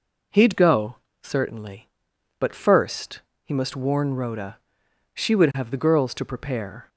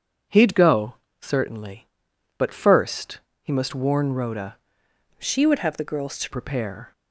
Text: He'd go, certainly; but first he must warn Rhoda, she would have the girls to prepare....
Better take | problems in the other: first | pauses between "first" and "he"; slight; at 3.2 s; 0.22 s long; slight in the first // changes voice from "she" to "to"; from 5.1 to 6.2 s; 1.1 s long

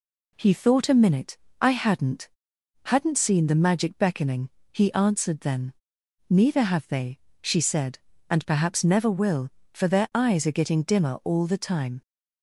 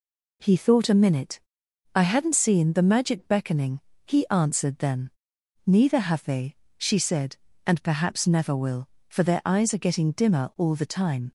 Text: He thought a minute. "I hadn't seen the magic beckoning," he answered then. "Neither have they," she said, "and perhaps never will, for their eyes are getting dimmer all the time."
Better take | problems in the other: second | says "hadn't" twice; at 2.8 s

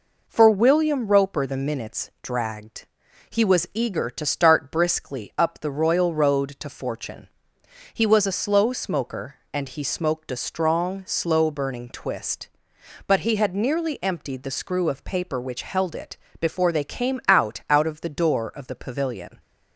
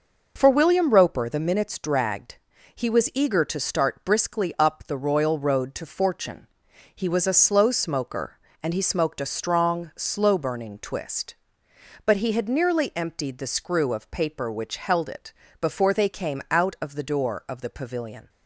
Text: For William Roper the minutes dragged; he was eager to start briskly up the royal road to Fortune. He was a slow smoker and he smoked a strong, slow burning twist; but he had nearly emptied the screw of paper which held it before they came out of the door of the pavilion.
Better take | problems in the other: second | pauses between "it" and "before"; slight; at 16.1 s; 0.24 s long; slight in the second // says "out" twice; at 17.6 s

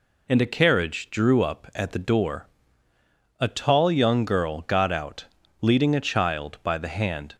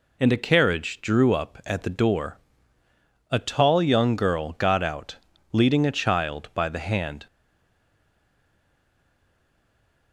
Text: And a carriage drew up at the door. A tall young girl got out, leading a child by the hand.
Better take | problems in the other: first | stays silent after the last word; strong; from 7.2 s on; 2.9 s long

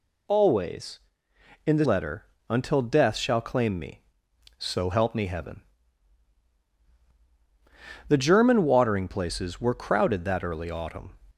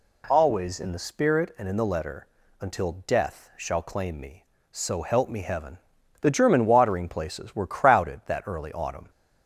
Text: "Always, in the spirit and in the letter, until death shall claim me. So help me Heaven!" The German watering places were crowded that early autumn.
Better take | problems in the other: second | skips "spirit and in the"; at 1.8 s

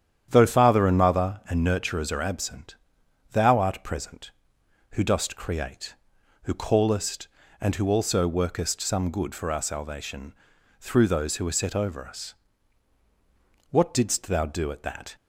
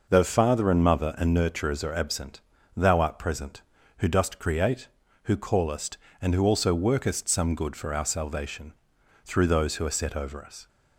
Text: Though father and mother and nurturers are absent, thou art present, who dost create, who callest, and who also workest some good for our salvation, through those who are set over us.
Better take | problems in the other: second | starts louder than the rest; strong; until 1.3 s; 9.5 dB // goes on to say "What didst thou do at that"; from 13.7 s on; 1.4 s long

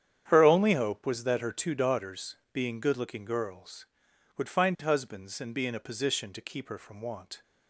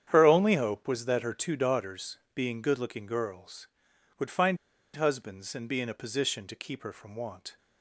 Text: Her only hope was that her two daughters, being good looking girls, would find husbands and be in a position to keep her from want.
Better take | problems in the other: first | starts louder than the rest; strong; until 1.0 s; 9 dB; strong in the first // pauses between "find" and "husbands"; at 4.5 s; 0.37 s long

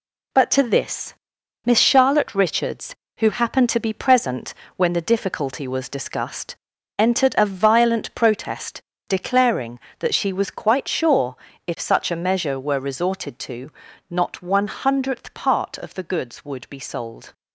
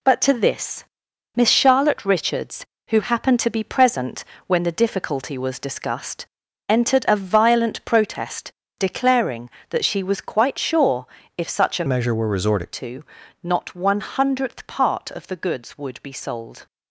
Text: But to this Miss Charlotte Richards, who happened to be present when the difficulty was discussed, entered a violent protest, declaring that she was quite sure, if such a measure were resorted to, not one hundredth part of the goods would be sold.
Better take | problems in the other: first | pauses between "this" and "Miss"; noticeable; at 0.8 s; 0.52 s long; noticeable in the first // pauses between "present" and "when"; slight; at 4.2 s; 0.24 s long; slight in the first // changes voice from "measure" to "resorted"; from 11.8 to 12.7 s; 0.9 s long

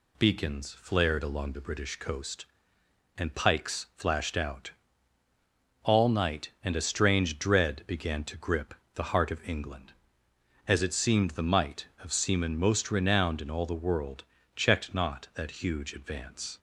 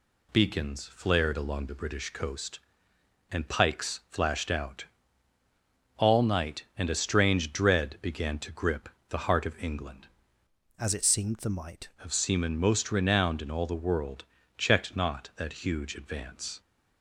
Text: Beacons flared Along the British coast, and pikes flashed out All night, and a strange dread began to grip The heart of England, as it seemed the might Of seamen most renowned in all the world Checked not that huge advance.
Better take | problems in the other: first | pauses between "out" and "All"; at 4.8 s; 1.1 s long; also in the first // pauses between "grip" and "The"; slight; at 8.8 s; 0.20 s long; slight in the first // changes voice from "as" to "might"; from 10.7 to 11.8 s; 1.1 s long // pauses between "world" and "Checked"; slight; at 14.2 s; 0.34 s long; slight in the first

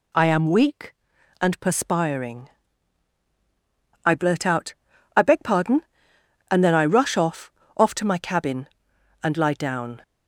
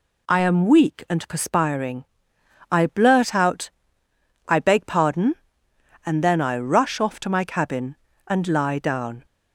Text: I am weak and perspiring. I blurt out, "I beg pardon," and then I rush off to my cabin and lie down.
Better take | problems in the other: second | says "off" twice; at 7.7 s

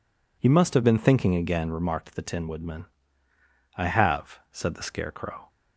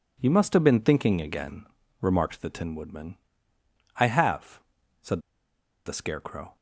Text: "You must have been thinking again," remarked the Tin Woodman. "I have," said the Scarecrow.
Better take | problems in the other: first | pauses between "said" and "the"; noticeable; at 5.2 s; 0.65 s long

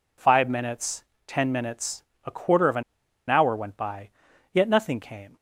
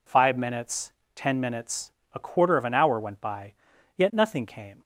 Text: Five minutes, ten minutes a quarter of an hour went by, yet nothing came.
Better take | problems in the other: second | pauses between "minutes" and "a"; slight; at 2.0 s; 0.22 s long; slight in the second // pauses between "an" and "hour"; noticeable; at 2.8 s; 0.46 s long

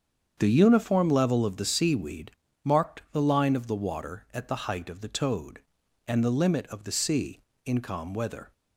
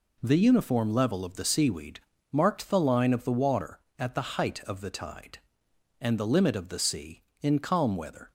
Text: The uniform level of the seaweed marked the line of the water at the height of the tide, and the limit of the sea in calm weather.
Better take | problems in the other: second | starts louder than the rest; strong; until 1.3 s; 7.5 dB // pauses between "seaweed" and "marked"; slight; at 2.3 s; 0.32 s long; slight in the second // says "toad" for "tide"; at 5.0 s

